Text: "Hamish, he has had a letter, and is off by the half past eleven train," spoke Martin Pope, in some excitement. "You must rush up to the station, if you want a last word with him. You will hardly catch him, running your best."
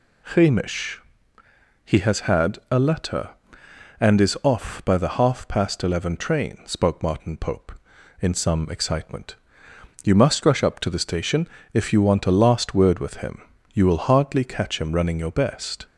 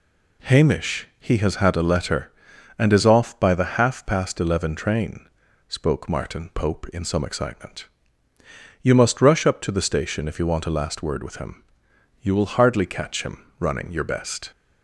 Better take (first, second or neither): neither